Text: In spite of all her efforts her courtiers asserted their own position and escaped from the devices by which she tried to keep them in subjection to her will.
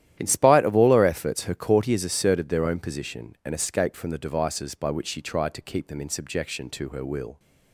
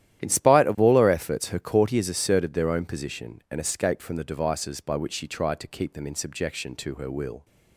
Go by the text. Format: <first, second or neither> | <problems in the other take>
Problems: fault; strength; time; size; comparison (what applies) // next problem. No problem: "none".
neither | starts louder than the rest; strong; the same in both